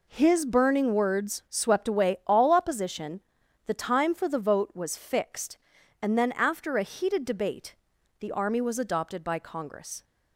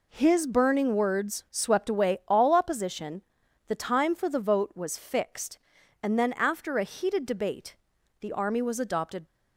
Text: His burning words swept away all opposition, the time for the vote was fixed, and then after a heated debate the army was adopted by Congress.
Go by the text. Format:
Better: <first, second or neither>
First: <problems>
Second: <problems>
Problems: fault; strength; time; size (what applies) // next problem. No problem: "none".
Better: first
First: pauses between "debate" and "the"; at 7.7 s; 0.44 s long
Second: pauses between "debate" and "the"; at 7.7 s; 0.44 s long // stops before "by Congress"; at 9.2 s